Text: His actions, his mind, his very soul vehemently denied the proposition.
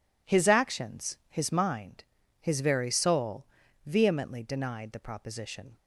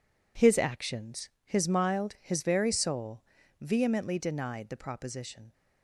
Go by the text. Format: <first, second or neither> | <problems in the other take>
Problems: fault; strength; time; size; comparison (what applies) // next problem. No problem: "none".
first | says "mild" for "mind"; at 1.6 s // pauses between "soul" and "vehemently"; slight; at 3.2 s; 0.36 s long; also in the first